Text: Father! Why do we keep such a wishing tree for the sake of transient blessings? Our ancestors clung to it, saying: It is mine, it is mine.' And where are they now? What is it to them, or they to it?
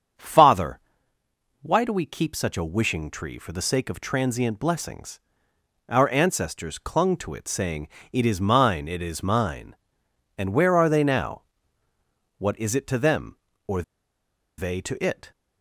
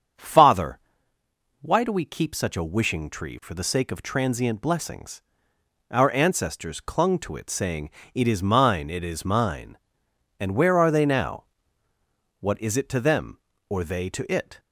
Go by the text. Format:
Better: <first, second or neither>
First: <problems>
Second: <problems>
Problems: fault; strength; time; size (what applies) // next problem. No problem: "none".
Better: second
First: starts louder than the rest; strong; until 2.0 s; 7.5 dB // pauses between "or" and "they"; noticeable; at 13.8 s; 0.74 s long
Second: starts louder than the rest; strong; until 1.9 s; 7.5 dB